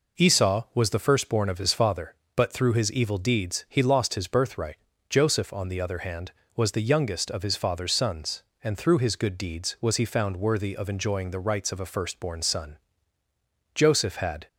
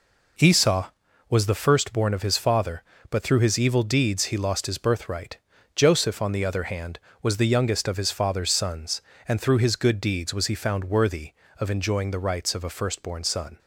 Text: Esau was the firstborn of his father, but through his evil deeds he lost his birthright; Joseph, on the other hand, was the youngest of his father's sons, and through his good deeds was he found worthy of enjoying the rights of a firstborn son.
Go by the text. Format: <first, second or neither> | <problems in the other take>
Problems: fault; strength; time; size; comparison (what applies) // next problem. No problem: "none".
second | goes on to say "Joseph had"; noticeable; from 13.7 s on; 0.74 s long